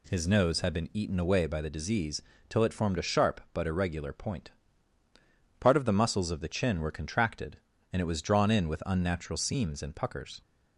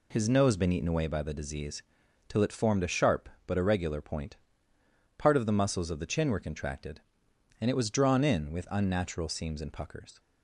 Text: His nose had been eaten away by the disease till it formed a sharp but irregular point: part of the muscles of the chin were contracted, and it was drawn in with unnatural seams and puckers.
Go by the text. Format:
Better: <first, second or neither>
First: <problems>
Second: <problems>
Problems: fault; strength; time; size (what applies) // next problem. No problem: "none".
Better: first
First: pauses between "disease" and "till"; slight; at 2.2 s; 0.26 s long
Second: skips "had"; at 0.5 s // pauses between "disease" and "till"; noticeable; at 1.8 s; 0.46 s long